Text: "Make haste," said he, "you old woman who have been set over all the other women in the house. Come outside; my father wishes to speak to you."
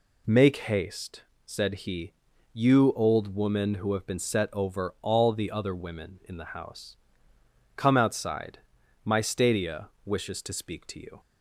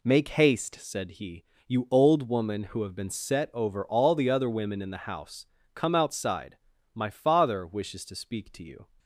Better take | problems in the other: second | says "stadia" for "father"; at 9.2 s

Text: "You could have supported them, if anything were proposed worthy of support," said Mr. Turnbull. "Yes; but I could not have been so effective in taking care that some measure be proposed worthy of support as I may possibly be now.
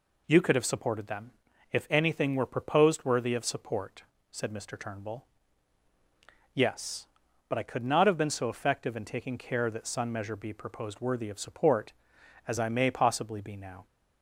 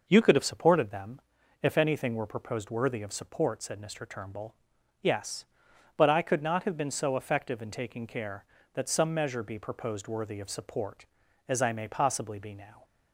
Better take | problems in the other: second | says "sun" for "some"; at 9.8 s

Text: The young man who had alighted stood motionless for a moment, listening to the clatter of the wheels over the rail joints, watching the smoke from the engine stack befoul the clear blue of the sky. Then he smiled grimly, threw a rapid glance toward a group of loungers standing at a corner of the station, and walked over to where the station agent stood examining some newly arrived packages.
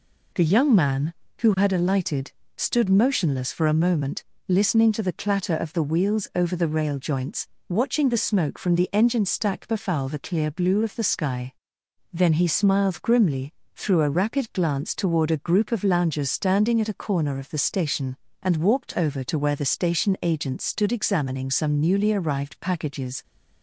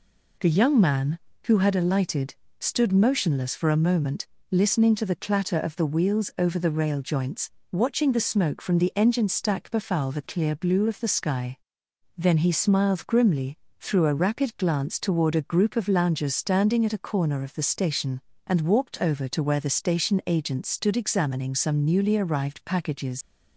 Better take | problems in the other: first | pauses between "alighted" and "stood"; slight; at 2.3 s; 0.24 s long; slight in the first // leaves "packages" unfinished; at 23.2 s; 65 ms

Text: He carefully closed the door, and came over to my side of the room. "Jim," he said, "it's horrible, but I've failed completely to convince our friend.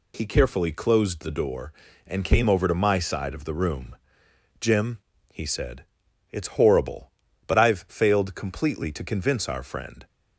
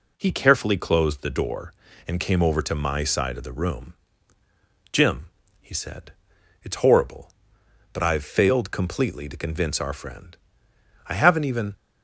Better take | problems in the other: first | goes on to say "I haven't even"; noticeable; from 11.0 s on; 0.68 s long

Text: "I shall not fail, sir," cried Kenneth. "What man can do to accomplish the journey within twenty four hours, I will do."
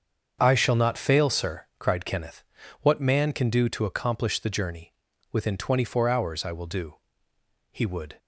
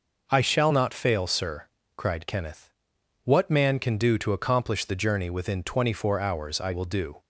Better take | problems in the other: second | starts louder than the rest; strong; until 1.4 s; 7 dB // pauses between "journey" and "within"; at 4.9 s; 0.38 s long // goes on to say "He would"; slight; from 7.7 s on; 0.46 s long

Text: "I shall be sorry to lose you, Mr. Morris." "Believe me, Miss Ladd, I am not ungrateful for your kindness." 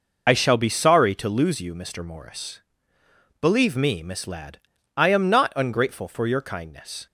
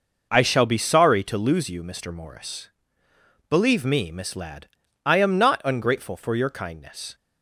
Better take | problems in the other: second | loses the start of "I"; at 0.2 s; 50 ms

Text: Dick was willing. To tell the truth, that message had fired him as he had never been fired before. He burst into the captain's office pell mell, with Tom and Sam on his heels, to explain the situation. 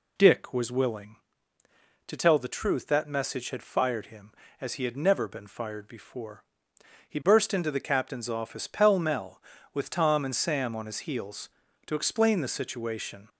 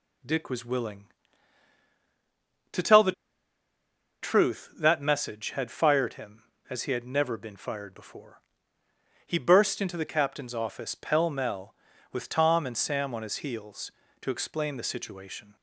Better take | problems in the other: first | pauses between "the" and "truth"; at 3.1 s; 1.1 s long

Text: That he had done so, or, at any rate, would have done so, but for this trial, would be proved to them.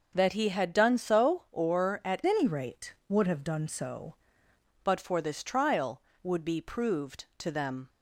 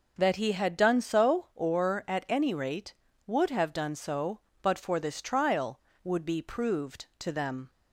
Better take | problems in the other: second | changes voice from "any" to "so"; from 2.2 to 4.1 s; 1.9 s long

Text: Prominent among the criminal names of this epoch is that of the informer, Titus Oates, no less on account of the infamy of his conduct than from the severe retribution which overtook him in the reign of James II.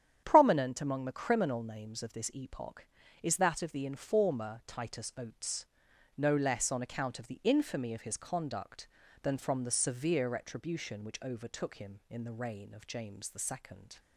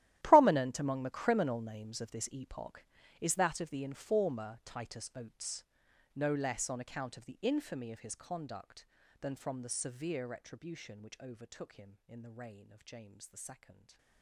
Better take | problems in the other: first | gets quieter; strong; throughout; 18 dB // starts louder than the rest; strong; until 1.2 s; 13.5 dB; strong in the first // stays silent after the last word; slight; from 13.7 s on; 0.5 s long

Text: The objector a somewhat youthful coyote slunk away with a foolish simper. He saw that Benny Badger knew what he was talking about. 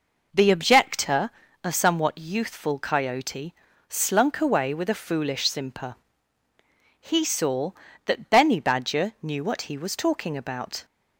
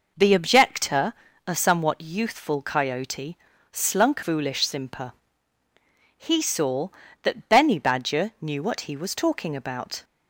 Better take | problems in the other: first | pauses between "objector" and "a"; slight; at 1.1 s; 0.36 s long; slight in the first // pauses between "coyote" and "slunk"; slight; at 3.3 s; 0.36 s long; slight in the first // skips "away with a"; at 4.2 s

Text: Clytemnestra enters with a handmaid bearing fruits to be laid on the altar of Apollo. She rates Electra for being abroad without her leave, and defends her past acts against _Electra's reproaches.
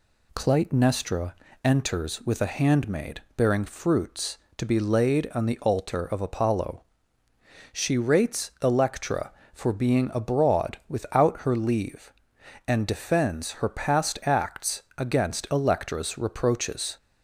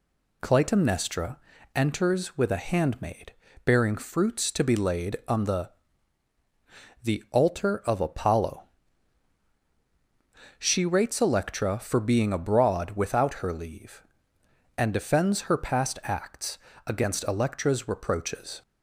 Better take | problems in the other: first | pauses between "Clytemnestra" and "enters"; at 1.3 s; 0.38 s long; slight in the first // pauses between "handmaid" and "bearing"; slight; at 3.3 s; 0.32 s long; slight in the first // says "the" twice; at 7.0 s // pauses between "acts" and "against"; slight; at 16.5 s; 0.28 s long

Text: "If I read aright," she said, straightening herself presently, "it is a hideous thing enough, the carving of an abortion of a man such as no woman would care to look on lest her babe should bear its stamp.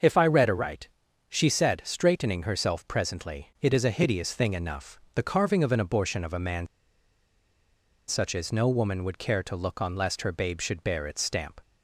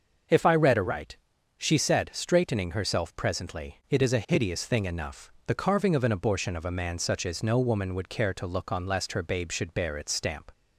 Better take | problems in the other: second | starts louder than the rest; until 1.4 s; 6 dB; also in the second // pauses between "man" and "such"; strong; at 6.6 s; 1.4 s long

